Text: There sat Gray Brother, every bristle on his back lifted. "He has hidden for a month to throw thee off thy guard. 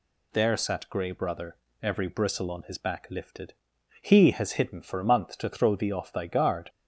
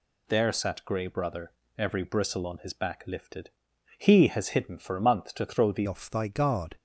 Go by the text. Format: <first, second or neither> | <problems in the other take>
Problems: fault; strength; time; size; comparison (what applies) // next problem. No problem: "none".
first | changes voice at "off"; from 5.8 s on; 0.9 s long